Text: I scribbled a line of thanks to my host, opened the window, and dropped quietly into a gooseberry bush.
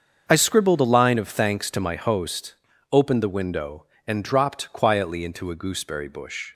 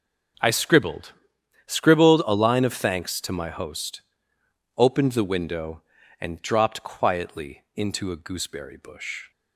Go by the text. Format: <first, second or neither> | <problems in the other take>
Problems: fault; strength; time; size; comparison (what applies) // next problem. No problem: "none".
first | starts louder than the rest; until 1.9 s; 6.5 dB; also in the first // says "scribbled" twice; at 1.6 s